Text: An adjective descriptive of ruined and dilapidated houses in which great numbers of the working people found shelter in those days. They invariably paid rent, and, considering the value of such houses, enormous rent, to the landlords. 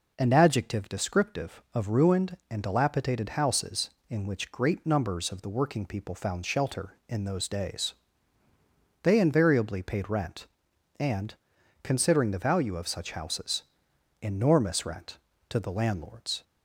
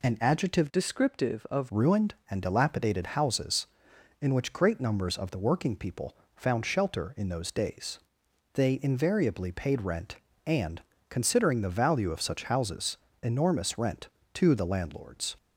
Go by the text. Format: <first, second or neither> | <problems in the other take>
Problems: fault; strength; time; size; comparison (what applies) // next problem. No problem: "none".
first | changes voice from "descriptive" to "of"; from 0.7 to 1.6 s; 0.9 s long // pauses between "people" and "found"; slight; at 6.1 s; 0.20 s long